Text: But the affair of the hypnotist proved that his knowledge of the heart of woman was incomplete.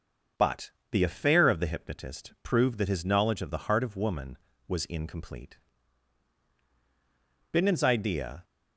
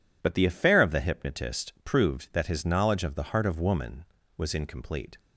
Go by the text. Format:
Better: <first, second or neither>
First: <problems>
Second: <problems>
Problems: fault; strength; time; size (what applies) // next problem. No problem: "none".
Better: second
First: starts louder than the rest; until 1.5 s; 6 dB // pauses between "But" and "the"; slight; at 0.7 s; 0.20 s long // goes on to say "Bindon's idea"; noticeable; from 7.5 s on; 0.92 s long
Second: none